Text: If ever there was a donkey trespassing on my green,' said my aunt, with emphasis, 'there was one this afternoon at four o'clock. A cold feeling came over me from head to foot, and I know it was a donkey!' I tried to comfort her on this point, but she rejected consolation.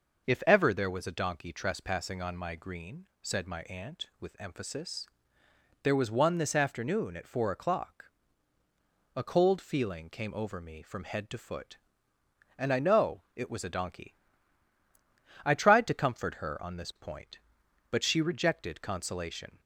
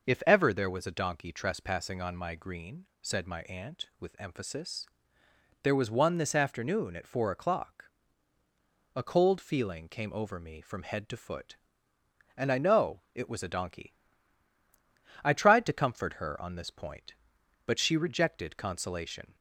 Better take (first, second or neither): neither